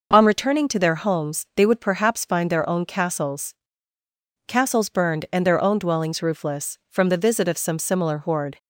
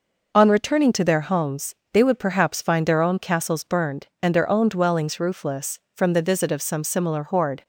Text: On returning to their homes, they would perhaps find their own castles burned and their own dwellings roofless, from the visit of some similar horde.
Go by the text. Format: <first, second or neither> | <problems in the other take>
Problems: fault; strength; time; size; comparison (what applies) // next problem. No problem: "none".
second | says "castles" twice; at 4.4 s